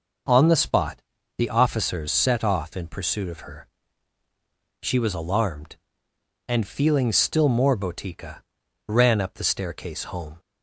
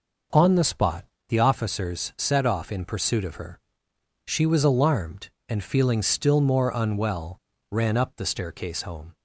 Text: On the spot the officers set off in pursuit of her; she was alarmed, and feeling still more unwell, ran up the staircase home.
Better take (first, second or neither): second